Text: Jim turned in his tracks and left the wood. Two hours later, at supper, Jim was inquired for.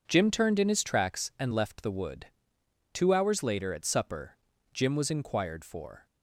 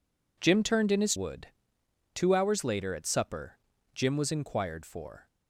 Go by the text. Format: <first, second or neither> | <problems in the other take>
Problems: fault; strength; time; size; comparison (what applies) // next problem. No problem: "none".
first | skips "tracks and left the"; at 1.1 s